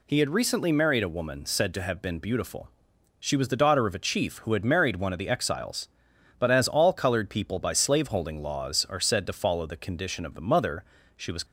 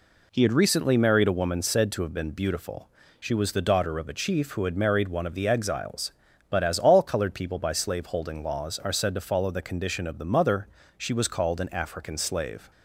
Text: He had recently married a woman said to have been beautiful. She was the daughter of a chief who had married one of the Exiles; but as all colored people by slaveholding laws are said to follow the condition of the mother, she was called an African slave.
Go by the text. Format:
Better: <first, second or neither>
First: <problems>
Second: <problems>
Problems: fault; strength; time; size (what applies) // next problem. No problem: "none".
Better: second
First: stops before "called an African slave"; at 11.4 s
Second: none